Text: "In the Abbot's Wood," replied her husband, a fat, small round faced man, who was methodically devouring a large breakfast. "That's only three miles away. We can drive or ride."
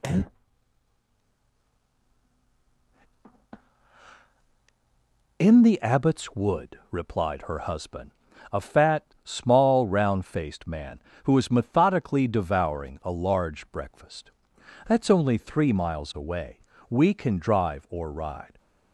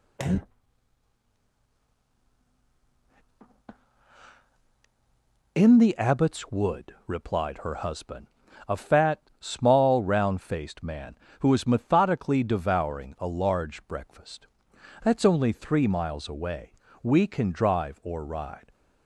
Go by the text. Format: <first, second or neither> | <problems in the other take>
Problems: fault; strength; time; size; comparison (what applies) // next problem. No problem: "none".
neither | none